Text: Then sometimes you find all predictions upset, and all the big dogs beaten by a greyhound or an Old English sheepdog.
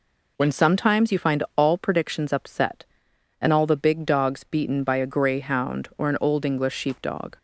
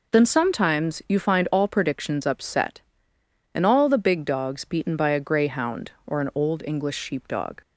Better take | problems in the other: second | says "When" for "Then"; at 0.3 s

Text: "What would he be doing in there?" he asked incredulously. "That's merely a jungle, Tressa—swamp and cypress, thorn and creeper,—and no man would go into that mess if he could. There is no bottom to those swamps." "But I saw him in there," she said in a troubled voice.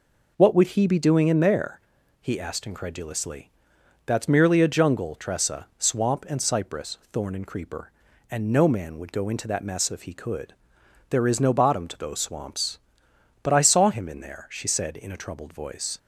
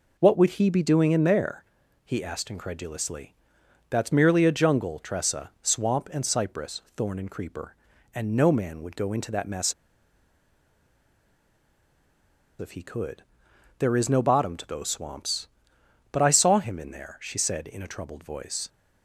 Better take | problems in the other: first | pauses between "mess" and "if"; strong; at 9.7 s; 2.8 s long

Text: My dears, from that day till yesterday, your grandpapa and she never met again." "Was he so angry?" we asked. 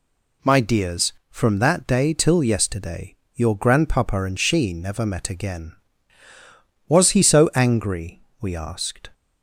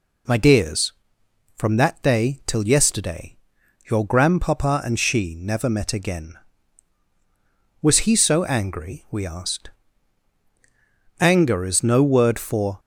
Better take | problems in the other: first | goes on to say "Anger is no word for"; from 11.1 s on; 1.6 s long

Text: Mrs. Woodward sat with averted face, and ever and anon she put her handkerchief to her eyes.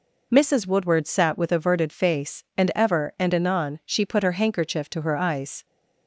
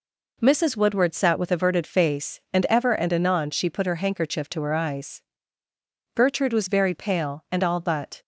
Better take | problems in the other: first | goes on to say "Gertrude was very pale and all but"; strong; from 6.1 s on; 2.0 s long

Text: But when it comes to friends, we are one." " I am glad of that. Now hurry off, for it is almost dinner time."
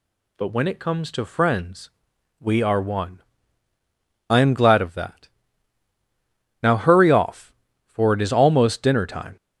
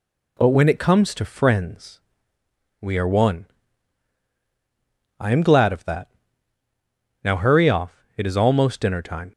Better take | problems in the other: first | skips "for"; at 8.1 s

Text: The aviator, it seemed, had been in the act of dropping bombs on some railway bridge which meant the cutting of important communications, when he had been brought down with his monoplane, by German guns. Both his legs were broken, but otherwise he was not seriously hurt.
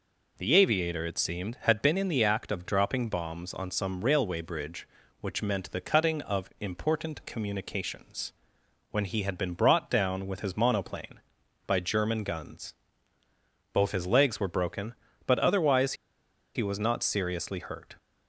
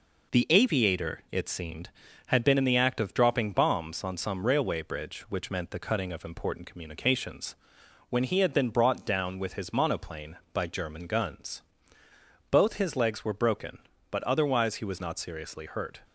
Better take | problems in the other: second | pauses between "otherwise" and "he"; noticeable; at 15.9 s; 0.62 s long

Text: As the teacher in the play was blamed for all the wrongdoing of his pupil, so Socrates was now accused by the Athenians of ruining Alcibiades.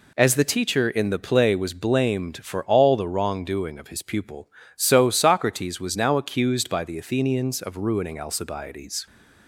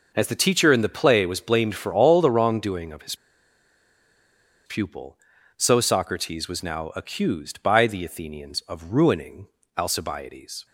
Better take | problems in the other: first | pauses between "his" and "pupil"; strong; at 3.1 s; 1.5 s long // pauses between "ruining" and "Alcibiades"; slight; at 9.4 s; 0.30 s long

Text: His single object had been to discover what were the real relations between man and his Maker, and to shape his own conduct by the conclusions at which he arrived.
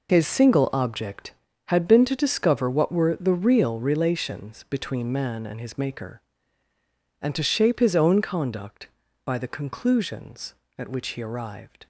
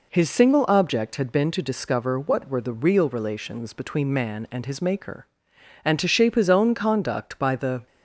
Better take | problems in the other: first | stops before "conclusions at which he arrived"; at 7.8 s

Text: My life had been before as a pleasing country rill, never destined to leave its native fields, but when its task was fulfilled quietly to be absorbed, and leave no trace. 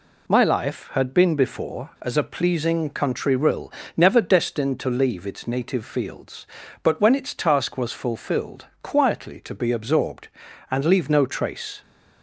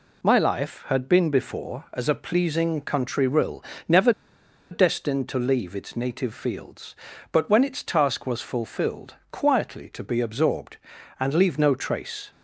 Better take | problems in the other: first | pauses between "never" and "destined"; noticeable; at 4.1 s; 0.60 s long // pauses between "fulfilled" and "quietly"; slight; at 9.1 s; 0.16 s long; slight in the first

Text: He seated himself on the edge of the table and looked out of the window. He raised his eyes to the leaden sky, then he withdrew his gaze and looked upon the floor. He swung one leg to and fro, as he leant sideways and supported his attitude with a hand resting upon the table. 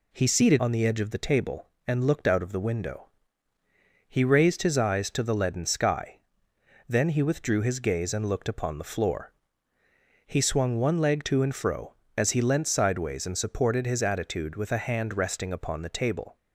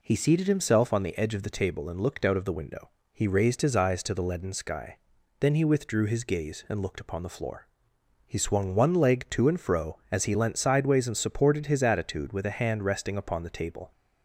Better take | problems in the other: second | skips "himself"; at 0.5 s

